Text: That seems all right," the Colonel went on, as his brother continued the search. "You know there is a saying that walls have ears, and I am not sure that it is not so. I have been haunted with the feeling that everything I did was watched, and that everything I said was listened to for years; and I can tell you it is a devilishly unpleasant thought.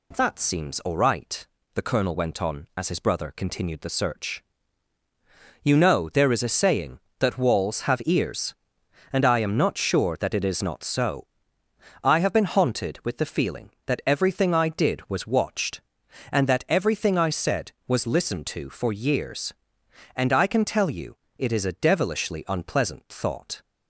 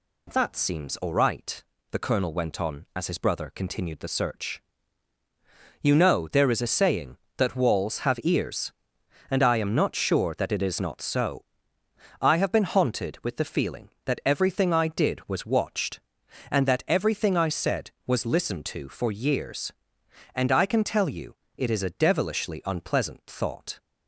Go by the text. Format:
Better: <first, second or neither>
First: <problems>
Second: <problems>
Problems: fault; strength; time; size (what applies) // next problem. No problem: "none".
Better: neither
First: pauses between "you" and "it"; slight; at 21.1 s; 0.20 s long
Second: pauses between "you" and "it"; slight; at 21.3 s; 0.20 s long